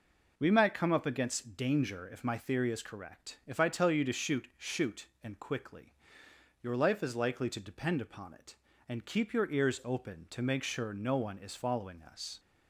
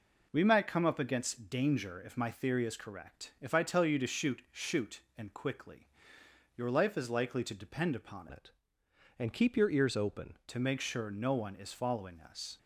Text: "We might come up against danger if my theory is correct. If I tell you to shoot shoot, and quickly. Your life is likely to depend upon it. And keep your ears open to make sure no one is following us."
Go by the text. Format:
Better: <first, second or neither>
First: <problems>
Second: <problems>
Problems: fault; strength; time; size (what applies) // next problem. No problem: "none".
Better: first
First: none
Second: changes voice from "it" to "open"; from 8.3 to 10.3 s; 2.0 s long